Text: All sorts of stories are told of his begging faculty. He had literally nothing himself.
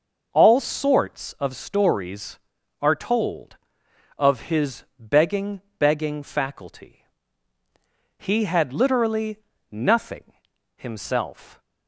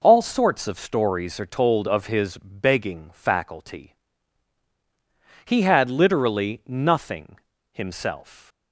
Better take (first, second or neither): second